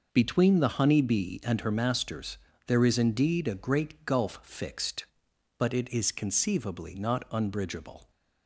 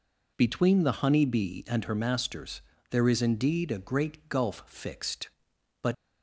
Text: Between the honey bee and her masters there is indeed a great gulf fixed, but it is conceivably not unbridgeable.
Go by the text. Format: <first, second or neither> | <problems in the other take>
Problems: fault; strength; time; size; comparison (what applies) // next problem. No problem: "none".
first | pauses between "masters" and "there"; slight; at 2.6 s; 0.28 s long; slight in the first // stops before "it is conceivably not unbridgeable"; at 5.9 s